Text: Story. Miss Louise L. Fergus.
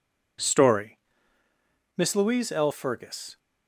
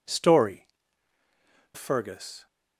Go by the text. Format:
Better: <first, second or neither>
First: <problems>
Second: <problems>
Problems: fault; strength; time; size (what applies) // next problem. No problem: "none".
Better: first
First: none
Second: skips "Miss Louise L"; at 1.2 s